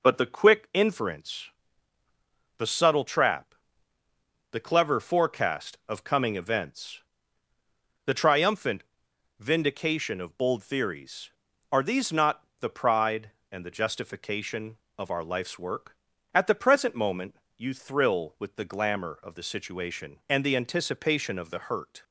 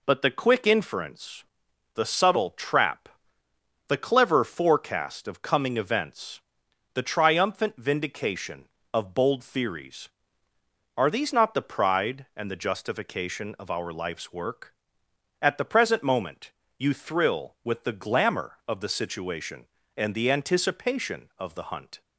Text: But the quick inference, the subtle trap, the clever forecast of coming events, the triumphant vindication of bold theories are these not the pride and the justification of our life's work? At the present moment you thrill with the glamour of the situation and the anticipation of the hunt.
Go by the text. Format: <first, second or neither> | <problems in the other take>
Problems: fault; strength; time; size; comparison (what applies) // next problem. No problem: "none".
second | pauses between "triumphant" and "vindication"; noticeable; at 8.8 s; 0.56 s long // pauses between "not" and "the"; slight; at 12.4 s; 0.16 s long // pauses between "moment" and "you"; slight; at 17.3 s; 0.20 s long; slight in the second // says "hurt" for "hunt"; at 21.5 s